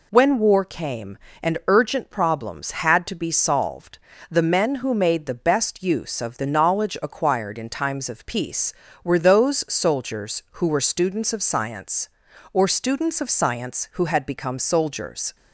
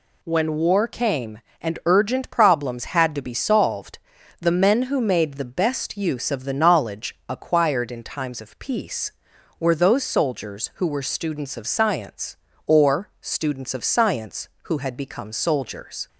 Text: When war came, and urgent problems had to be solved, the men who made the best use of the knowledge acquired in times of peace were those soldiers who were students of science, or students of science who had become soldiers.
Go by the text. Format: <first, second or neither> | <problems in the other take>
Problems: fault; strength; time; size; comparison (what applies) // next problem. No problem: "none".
neither | none